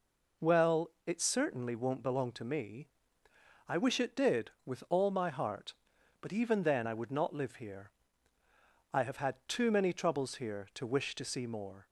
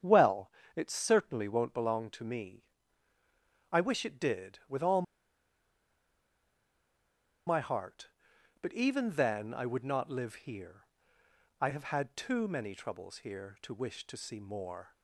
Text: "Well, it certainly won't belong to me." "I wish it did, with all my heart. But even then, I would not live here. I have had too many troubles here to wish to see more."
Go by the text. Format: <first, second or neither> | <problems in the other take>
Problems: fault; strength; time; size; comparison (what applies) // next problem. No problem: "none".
first | starts louder than the rest; strong; until 1.2 s; 8.5 dB // pauses between "all" and "my"; strong; at 5.0 s; 2.4 s long